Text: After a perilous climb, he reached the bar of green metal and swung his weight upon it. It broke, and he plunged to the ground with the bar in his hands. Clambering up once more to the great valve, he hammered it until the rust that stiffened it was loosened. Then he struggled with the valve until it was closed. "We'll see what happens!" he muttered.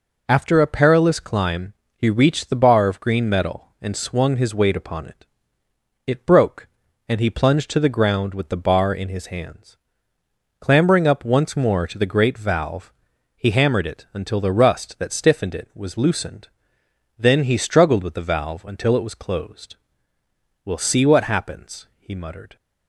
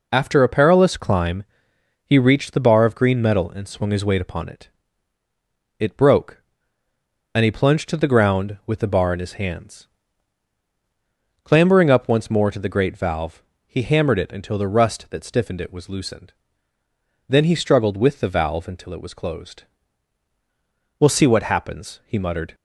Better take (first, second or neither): neither